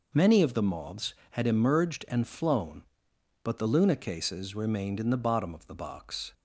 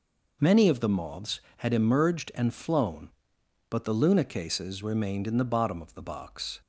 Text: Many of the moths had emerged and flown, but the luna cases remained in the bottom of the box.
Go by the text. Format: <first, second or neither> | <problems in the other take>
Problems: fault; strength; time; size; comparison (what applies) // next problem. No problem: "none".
neither | none